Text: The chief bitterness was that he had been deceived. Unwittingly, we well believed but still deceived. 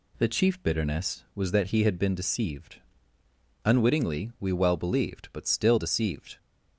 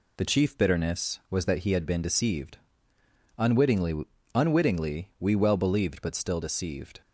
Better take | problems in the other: first | says "Unwittingly" twice; at 4.3 s

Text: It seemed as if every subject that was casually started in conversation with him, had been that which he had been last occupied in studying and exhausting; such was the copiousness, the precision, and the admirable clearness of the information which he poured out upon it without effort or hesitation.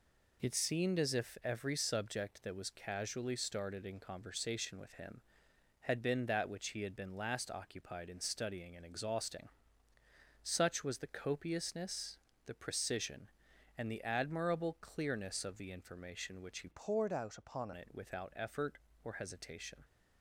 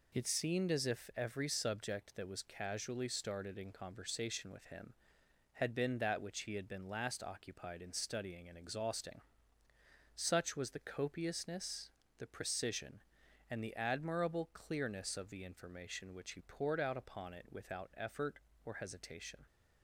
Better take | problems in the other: second | changes voice from "poured" to "upon"; from 16.7 to 17.7 s; 1.0 s long

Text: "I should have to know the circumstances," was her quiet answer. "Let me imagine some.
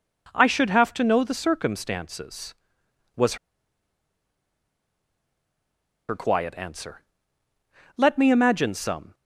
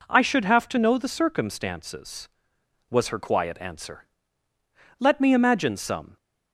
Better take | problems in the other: second | pauses between "was" and "her"; strong; at 3.3 s; 2.7 s long

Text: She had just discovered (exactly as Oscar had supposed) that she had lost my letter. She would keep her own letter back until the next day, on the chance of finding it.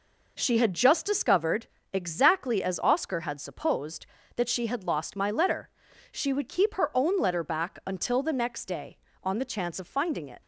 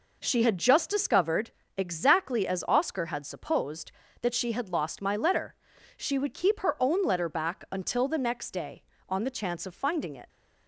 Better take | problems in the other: neither | none

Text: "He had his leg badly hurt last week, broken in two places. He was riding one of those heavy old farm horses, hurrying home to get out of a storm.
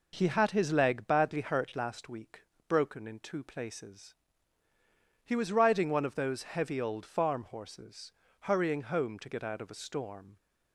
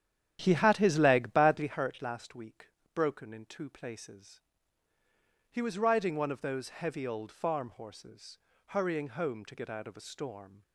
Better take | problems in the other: first | starts louder than the rest; strong; until 1.7 s; 10 dB

